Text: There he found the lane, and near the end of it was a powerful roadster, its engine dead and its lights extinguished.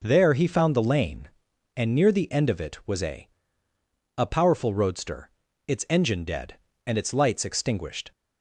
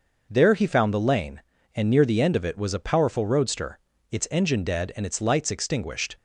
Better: second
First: says "a" twice; at 4.1 s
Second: none

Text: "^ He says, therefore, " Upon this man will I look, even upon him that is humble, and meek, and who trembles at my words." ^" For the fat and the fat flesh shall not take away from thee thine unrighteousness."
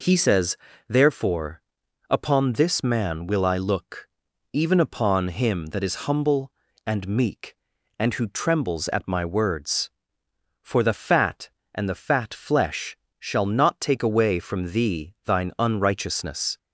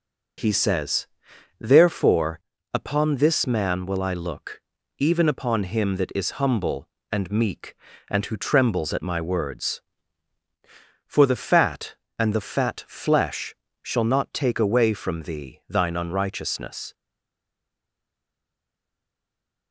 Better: first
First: pauses between "flesh" and "shall"; slight; at 12.9 s; 0.22 s long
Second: starts louder than the rest; noticeable; until 1.9 s; 6 dB // pauses between "flesh" and "shall"; slight; at 13.5 s; 0.30 s long // stays silent after the last word; strong; from 16.9 s on; 2.8 s long

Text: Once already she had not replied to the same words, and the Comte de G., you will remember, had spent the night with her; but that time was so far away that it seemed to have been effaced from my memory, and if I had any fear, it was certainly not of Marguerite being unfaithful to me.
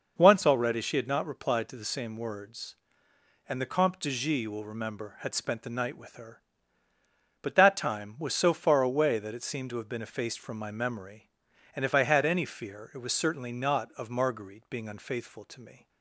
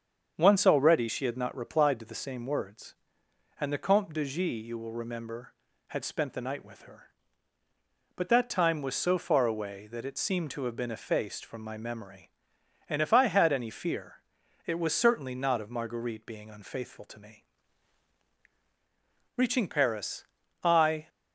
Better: first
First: none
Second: starts louder than the rest; until 1.3 s; 7 dB // goes on to say "Reaching Paris I"; strong; from 19.3 s on; 1.7 s long

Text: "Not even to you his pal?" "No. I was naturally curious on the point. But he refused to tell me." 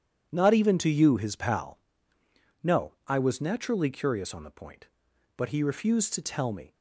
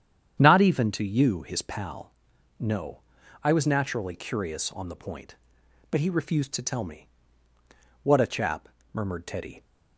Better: first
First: none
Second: starts louder than the rest; strong; until 1.4 s; 9 dB // goes on to say "What a chap murmured Teddy"; from 8.0 s on; 1.6 s long

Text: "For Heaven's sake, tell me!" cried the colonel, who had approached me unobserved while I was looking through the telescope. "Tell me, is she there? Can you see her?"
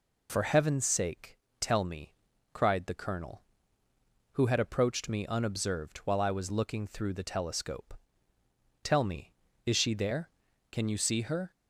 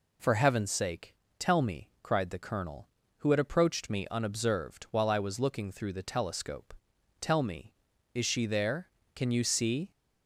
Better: first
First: none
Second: stops before "her"; at 9.9 s

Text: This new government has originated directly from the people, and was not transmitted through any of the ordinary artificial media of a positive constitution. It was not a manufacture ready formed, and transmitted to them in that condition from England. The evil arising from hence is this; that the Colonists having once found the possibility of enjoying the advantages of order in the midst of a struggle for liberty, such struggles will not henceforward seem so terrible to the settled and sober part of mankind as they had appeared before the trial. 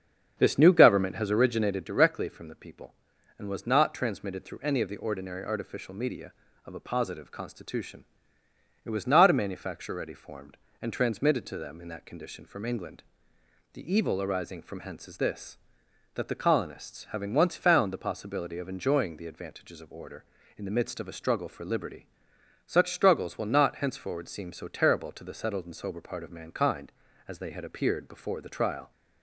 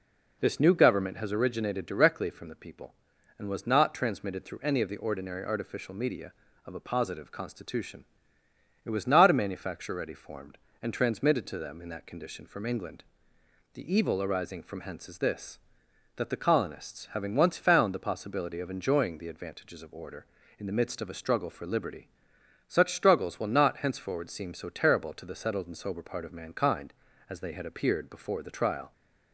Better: second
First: starts louder than the rest; strong; until 1.9 s; 7.5 dB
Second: none

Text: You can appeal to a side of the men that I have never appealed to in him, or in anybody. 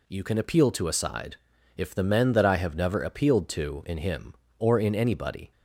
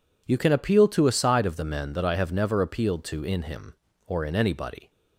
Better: second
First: says "if" for "of"; at 1.7 s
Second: none

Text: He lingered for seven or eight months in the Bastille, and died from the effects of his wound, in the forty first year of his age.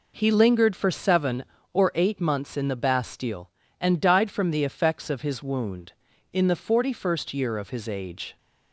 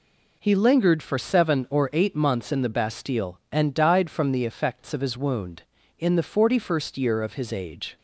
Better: neither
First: none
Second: none

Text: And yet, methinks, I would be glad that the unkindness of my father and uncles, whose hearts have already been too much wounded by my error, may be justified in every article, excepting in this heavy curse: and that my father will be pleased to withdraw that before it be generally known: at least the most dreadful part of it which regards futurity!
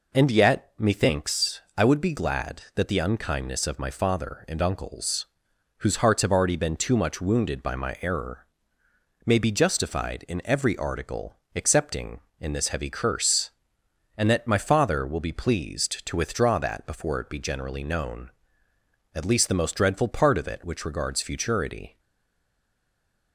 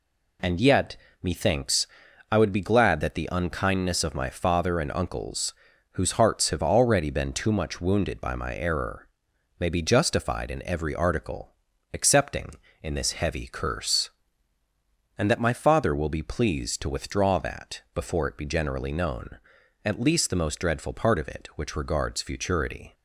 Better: second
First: stays silent after the last word; noticeable; from 21.9 s on; 1.4 s long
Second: none

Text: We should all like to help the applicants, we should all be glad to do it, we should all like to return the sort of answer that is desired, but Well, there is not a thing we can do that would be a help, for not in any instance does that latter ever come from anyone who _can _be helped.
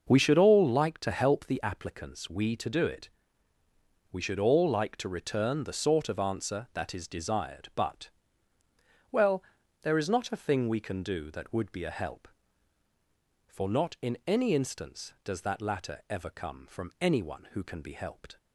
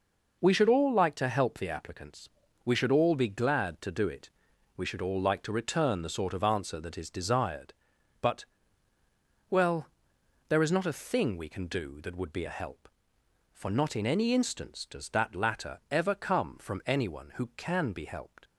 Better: second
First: skips "should all be glad"; at 2.5 s // pauses between "but" and "Well"; at 8.0 s; 1.0 s long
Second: pauses between "but" and "Well"; at 8.4 s; 1.0 s long

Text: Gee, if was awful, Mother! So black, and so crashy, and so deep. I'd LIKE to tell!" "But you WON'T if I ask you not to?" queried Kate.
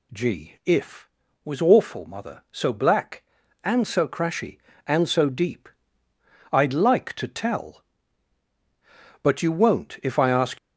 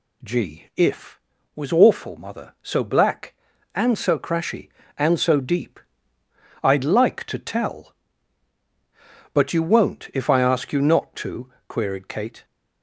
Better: second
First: stops before "you not to queried Kate"; at 10.5 s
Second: none

